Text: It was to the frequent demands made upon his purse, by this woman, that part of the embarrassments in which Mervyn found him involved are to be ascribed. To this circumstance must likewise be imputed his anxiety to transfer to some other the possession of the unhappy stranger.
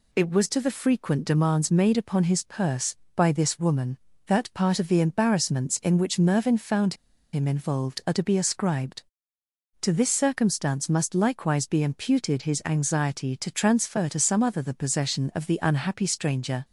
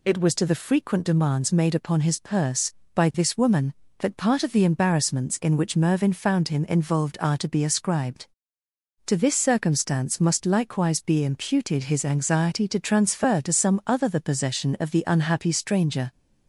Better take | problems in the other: second | pauses between "found" and "him"; at 6.9 s; 0.39 s long

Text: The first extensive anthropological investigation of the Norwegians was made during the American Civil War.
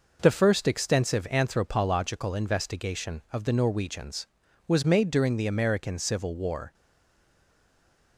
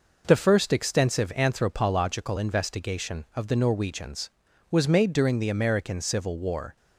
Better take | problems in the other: second | stays silent after the last word; noticeable; from 6.7 s on; 1.4 s long

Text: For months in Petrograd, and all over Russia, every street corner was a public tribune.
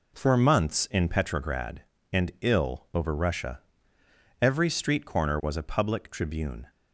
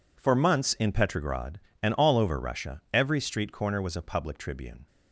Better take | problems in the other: second | says "ill" for "all"; at 2.4 s

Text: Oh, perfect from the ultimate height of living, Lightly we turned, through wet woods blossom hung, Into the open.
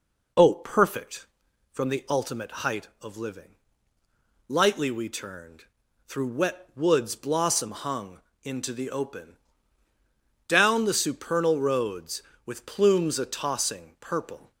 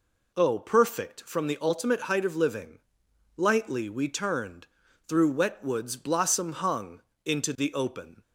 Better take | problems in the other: second | goes on to say "Down the supernal roads With plumes a tossing purple"; strong; from 10.4 s on; 4.0 s long

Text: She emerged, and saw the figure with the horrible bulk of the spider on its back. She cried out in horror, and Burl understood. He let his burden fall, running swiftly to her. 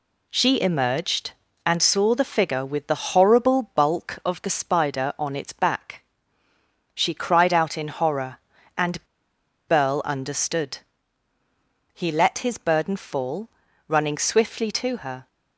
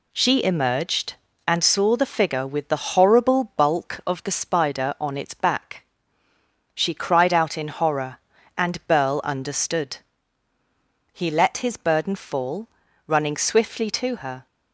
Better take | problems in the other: second | pauses between "and" and "Burl"; noticeable; at 9.0 s; 0.63 s long

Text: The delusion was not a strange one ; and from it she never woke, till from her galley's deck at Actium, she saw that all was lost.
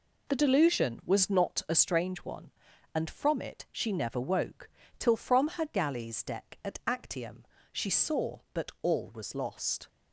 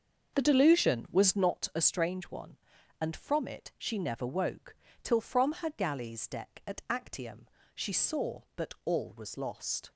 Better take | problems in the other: first | starts louder than the rest; until 1.5 s; 6.5 dB

